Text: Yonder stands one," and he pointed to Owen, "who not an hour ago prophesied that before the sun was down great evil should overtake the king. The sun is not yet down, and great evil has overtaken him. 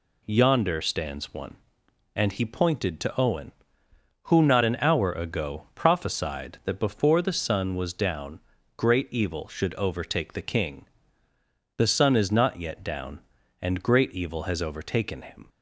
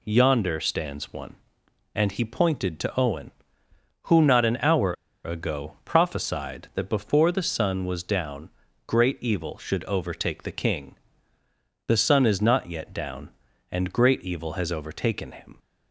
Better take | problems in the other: first | pauses between "hour" and "ago"; slight; at 4.9 s; 0.32 s long // pauses between "down" and "great"; at 8.4 s; 0.38 s long; also in the first

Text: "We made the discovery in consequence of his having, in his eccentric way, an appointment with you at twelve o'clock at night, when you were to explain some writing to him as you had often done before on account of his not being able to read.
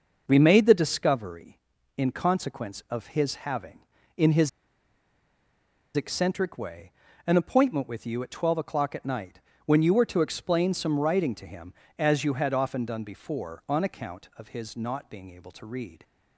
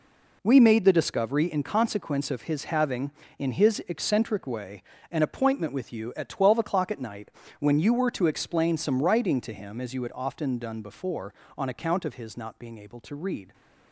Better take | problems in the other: second | pauses between "his" and "eccentric"; strong; at 4.4 s; 1.4 s long

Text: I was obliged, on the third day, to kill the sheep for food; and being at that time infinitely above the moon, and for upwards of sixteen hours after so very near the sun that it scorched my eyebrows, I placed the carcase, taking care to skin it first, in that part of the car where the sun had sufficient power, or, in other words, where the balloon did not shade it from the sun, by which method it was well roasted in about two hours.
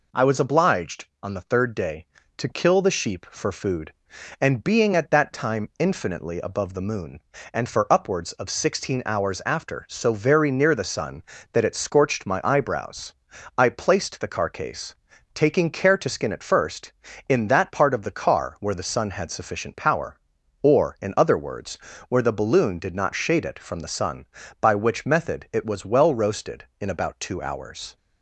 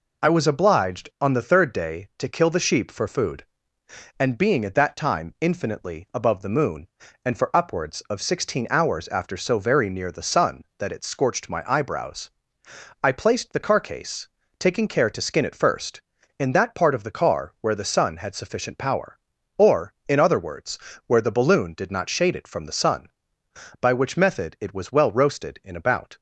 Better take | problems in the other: first | stops before "two hours"; at 26.1 s

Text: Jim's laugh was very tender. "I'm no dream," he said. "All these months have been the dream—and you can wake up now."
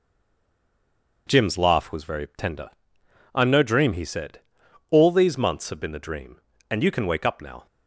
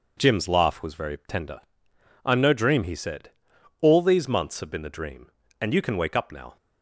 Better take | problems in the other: second | stays silent before the first word; noticeable; until 1.2 s; 1.2 s long

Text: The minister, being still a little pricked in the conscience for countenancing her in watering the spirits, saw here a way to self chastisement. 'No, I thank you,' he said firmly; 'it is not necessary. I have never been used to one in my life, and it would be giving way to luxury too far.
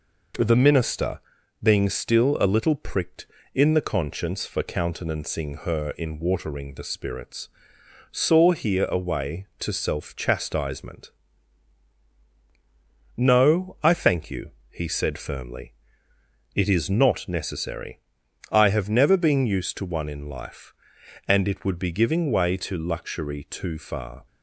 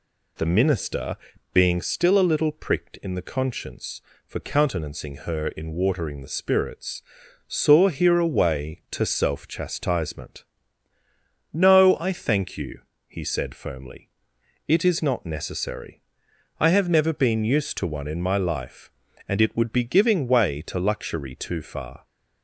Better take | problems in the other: second | skips "my"; at 20.2 s

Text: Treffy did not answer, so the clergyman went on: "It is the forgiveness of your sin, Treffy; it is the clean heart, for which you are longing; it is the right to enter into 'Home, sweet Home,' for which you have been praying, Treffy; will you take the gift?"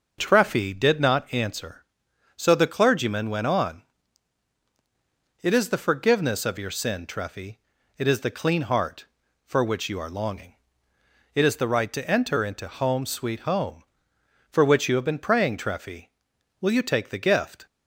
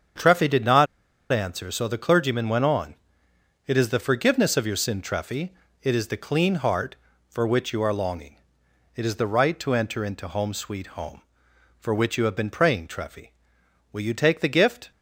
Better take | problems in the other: first | starts louder than the rest; strong; until 1.6 s; 7 dB; noticeable in the first // pauses between "not" and "answer"; noticeable; at 0.8 s; 0.46 s long

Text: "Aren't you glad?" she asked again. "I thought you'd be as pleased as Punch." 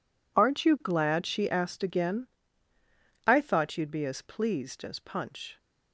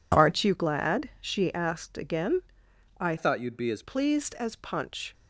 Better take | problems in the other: first | changes voice from "thought" to "as"; from 3.1 to 3.8 s; 0.7 s long

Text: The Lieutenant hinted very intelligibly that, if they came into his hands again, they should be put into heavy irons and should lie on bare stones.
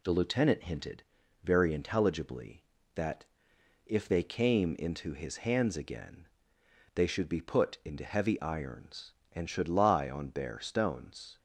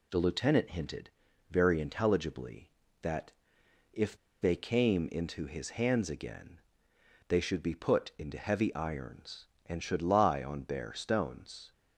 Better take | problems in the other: first | pauses between "hinted" and "very"; at 1.0 s; 0.40 s long; also in the first // pauses between "if" and "they"; slight; at 4.1 s; 0.25 s long

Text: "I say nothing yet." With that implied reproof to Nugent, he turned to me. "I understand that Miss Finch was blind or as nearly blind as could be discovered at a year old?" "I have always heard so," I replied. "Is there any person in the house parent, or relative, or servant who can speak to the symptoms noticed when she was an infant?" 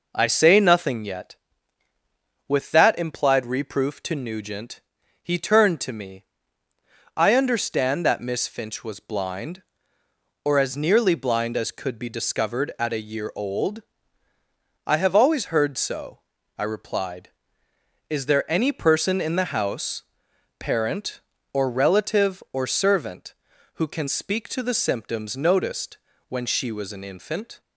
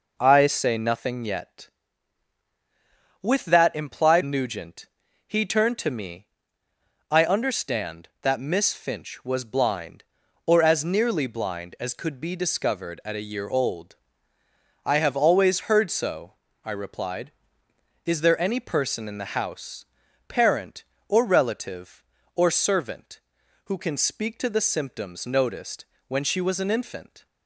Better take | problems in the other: first | skips "reproof to"; at 4.2 s // pauses between "house" and "parent"; at 19.8 s; 0.44 s long; noticeable in the first // pauses between "noticed" and "when"; slight; at 25.8 s; 0.24 s long; slight in the first

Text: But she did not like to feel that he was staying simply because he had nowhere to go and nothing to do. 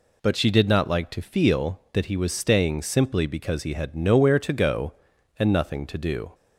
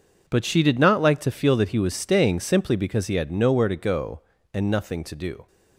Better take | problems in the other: first | gets quieter; strong; throughout; 11.5 dB

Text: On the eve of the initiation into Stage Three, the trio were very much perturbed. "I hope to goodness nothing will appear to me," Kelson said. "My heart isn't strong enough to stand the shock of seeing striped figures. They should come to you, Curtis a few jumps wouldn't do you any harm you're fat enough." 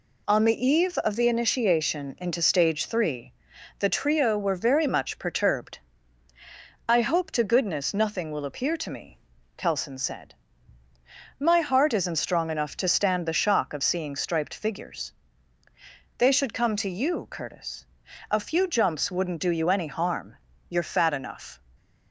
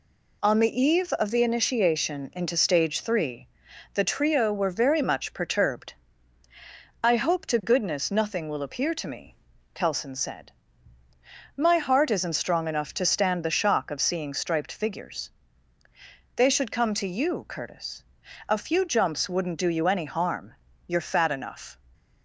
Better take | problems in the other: neither | pauses between "Curtis" and "a"; noticeable; the same in both // pauses between "harm" and "you're"; slight; the same in both

